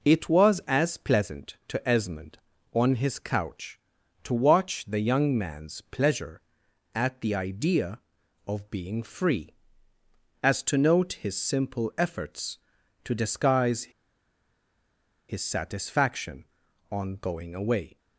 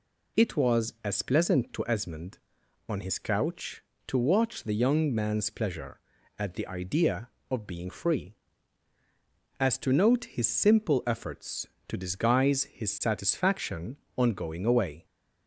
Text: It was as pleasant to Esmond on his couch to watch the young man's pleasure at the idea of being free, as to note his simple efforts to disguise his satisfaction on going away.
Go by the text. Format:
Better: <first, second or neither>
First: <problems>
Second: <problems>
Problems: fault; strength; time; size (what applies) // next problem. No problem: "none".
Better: second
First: pauses between "disguise" and "his"; strong; at 13.8 s; 1.4 s long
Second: none